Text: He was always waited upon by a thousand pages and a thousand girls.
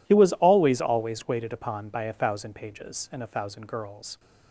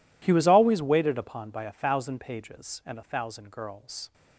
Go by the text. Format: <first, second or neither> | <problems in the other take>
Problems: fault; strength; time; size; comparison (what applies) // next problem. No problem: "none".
second | says "always" twice; at 0.7 s